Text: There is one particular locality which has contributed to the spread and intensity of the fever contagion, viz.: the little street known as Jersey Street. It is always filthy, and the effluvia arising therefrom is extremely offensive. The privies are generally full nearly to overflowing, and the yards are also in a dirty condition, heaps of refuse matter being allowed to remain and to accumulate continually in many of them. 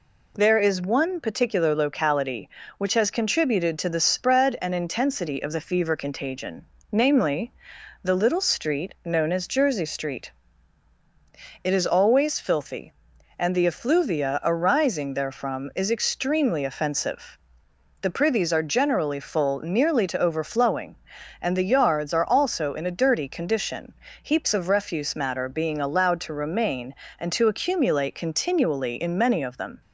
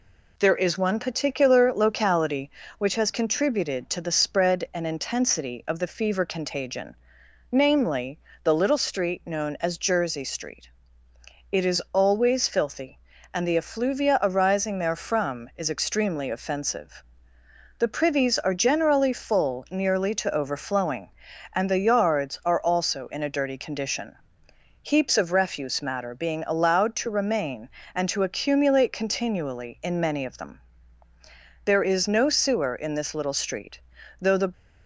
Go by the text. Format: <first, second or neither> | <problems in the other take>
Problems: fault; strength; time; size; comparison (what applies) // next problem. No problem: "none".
first | goes on to say "There is no sewer in this little street though the"; strong; from 31.6 s on; 2.8 s long